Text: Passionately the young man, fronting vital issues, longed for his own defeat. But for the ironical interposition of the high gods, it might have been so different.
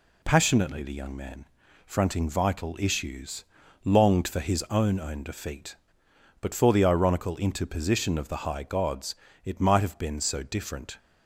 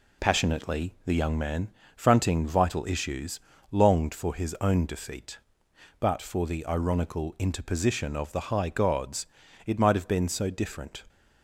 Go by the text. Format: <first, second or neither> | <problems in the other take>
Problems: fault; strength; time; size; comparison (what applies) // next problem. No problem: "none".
second | says "own" twice; at 4.9 s